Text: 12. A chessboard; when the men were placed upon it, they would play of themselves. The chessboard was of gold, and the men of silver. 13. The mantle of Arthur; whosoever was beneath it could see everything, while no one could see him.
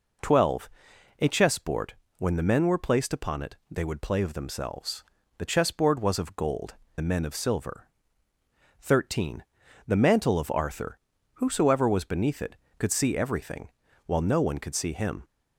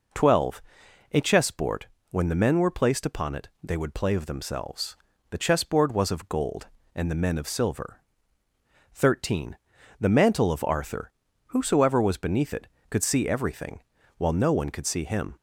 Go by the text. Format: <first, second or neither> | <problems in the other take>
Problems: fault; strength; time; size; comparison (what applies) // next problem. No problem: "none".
second | skips "and"; at 6.8 s